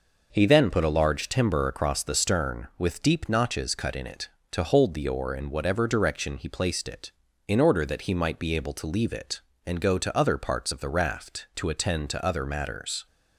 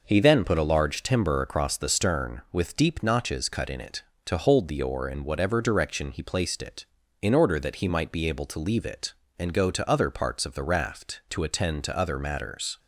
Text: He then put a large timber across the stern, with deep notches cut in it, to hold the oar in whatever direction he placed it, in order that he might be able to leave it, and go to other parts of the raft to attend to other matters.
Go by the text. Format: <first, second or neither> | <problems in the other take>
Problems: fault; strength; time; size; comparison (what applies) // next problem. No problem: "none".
neither | none